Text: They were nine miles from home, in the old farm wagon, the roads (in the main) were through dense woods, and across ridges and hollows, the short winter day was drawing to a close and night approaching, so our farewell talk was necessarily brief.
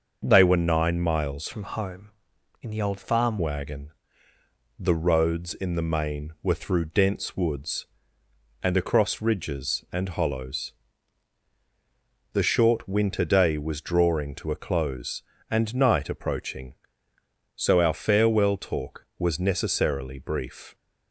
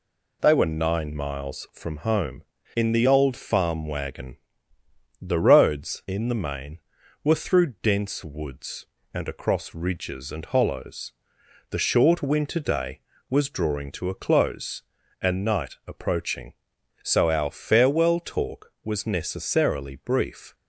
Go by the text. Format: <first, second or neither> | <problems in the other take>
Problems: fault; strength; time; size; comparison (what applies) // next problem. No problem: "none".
second | starts louder than the rest; until 1.2 s; 6 dB // changes voice from "from" to "farm"; from 1.5 to 3.3 s; 1.8 s long